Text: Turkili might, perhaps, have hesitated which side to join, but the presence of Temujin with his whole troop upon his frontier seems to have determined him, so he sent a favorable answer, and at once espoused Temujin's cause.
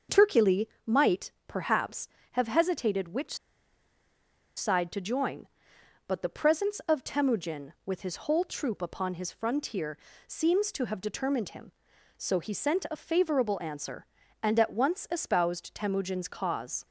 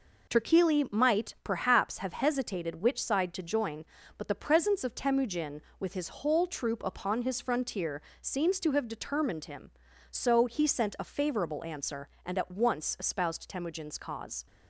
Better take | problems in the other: second | starts louder than the rest; until 1.2 s; 6.5 dB // pauses between "Turkili" and "might"; slight; at 0.6 s; 0.18 s long // pauses between "which" and "side"; at 3.3 s; 1.2 s long // pauses between "frontier" and "seems"; slight; at 9.9 s; 0.30 s long; slight in the second

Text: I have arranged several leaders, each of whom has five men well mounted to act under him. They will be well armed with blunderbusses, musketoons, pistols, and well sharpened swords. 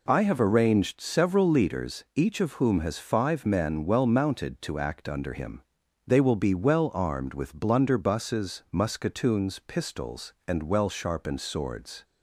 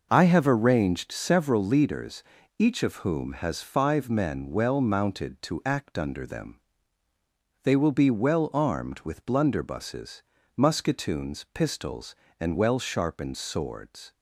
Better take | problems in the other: first | says "them" for "him"; at 6.2 s

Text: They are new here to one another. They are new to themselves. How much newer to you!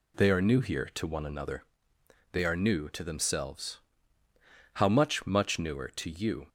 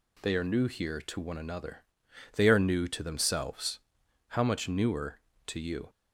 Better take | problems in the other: second | says "much" twice; at 5.2 s

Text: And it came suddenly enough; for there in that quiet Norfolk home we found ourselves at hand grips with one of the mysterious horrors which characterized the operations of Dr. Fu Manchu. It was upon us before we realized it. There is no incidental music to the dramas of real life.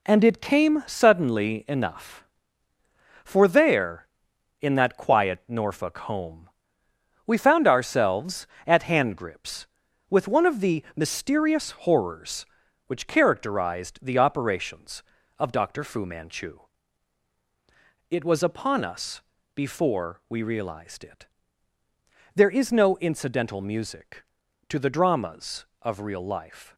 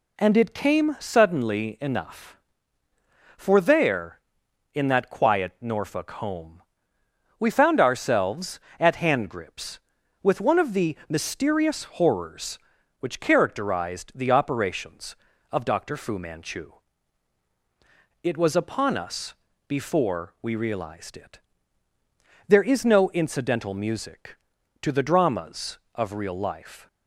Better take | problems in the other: second | gets quieter; throughout; 6.5 dB // pauses between "home" and "we"; noticeable; at 6.4 s; 0.78 s long; noticeable in the second // pauses between "us" and "before"; slight; at 19.2 s; 0.34 s long; slight in the second

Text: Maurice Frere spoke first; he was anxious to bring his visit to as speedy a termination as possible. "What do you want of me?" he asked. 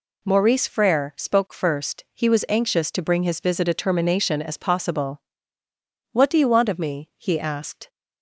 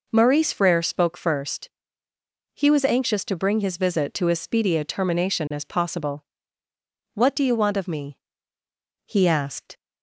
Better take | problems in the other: second | skips "to as speedy"; at 3.6 s

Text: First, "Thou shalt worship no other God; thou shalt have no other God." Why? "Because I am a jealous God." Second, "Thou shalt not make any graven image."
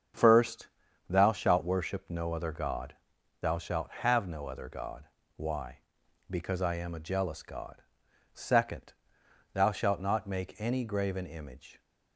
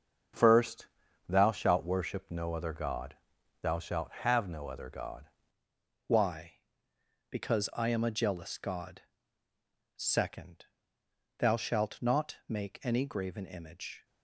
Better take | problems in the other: first | starts louder than the rest; until 1.7 s; 7 dB; strong in the first // changes voice at "Why"; from 6.0 s on; 8.0 s long

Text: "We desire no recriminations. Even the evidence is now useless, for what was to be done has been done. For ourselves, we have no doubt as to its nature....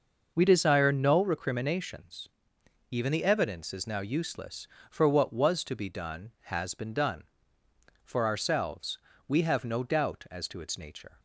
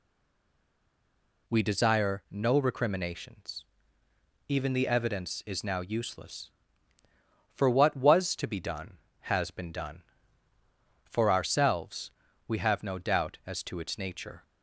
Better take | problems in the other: first | stays silent before the first word; noticeable; until 1.4 s; 1.4 s long

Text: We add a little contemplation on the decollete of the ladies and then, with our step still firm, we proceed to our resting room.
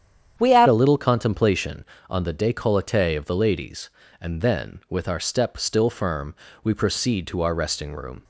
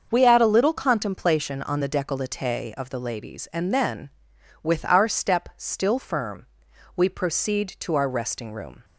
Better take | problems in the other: second | starts louder than the rest; strong; until 1.4 s; 9 dB; also in the second // changes voice at "a"; from 0.6 s on; 7.6 s long

